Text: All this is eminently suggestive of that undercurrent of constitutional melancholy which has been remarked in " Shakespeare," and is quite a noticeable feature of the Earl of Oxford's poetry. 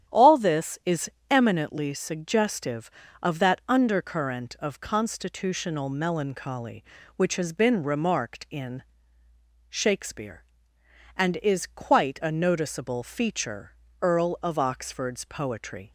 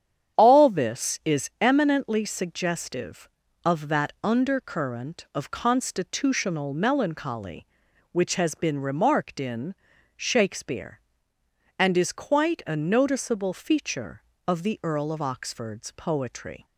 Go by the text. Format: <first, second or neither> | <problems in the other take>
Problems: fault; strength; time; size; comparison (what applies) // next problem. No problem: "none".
second | starts louder than the rest; strong; until 1.3 s; 10.5 dB; strong in the second // pauses between "is" and "eminently"; slight; at 1.0 s; 0.20 s long // skips "of the"; at 13.8 s